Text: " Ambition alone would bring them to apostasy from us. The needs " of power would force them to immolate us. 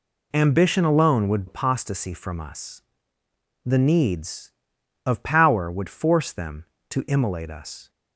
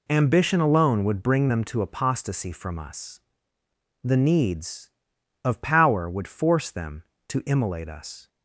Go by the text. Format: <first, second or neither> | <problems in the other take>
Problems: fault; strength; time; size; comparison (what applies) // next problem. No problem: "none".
second | skips "bring them to"; at 1.4 s